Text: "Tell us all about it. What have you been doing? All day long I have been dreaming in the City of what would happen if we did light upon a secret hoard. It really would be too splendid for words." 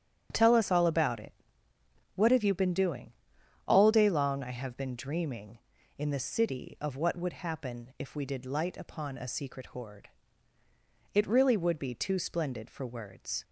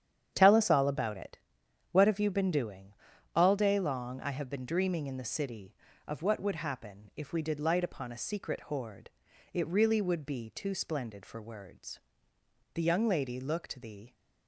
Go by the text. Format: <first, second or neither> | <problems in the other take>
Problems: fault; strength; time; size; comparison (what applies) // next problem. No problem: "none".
first | starts louder than the rest; strong; until 1.3 s; 9 dB; strong in the first // goes on to say "The young lady looked the"; from 12.7 s on; 1.4 s long